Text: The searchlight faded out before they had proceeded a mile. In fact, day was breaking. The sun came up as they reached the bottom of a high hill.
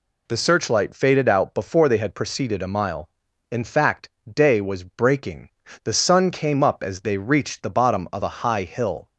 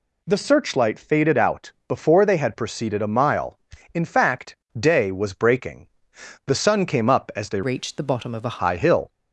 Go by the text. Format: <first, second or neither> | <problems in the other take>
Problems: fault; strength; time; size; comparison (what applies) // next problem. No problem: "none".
first | pauses between "out" and "before"; slight; at 1.7 s; 0.16 s long // changes voice from "reached" to "a"; from 7.6 to 8.5 s; 0.9 s long